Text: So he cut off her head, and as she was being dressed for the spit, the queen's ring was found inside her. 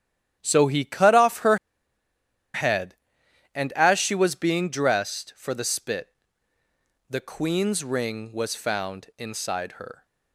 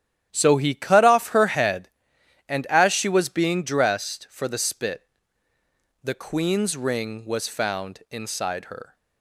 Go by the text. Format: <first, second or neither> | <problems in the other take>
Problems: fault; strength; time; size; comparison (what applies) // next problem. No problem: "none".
second | starts louder than the rest; strong; until 1.4 s; 11 dB; strong in the second // pauses between "her" and "head"; noticeable; at 1.5 s; 0.96 s long